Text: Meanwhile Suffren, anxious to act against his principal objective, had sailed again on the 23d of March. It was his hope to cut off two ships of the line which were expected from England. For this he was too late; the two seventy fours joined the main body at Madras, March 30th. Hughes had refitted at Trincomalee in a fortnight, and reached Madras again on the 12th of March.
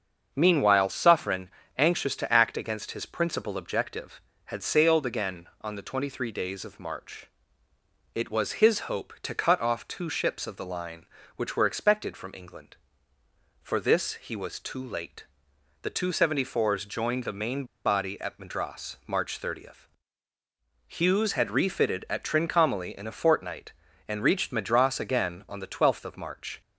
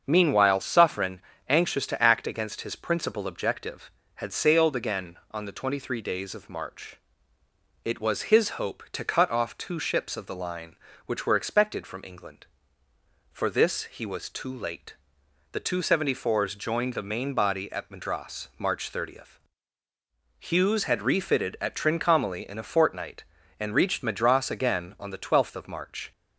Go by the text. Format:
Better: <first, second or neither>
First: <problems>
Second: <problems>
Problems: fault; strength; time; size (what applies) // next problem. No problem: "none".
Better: second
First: starts louder than the rest; until 1.3 s; 7 dB // pauses between "main" and "body"; slight; at 17.6 s; 0.21 s long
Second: starts louder than the rest; until 1.0 s; 7 dB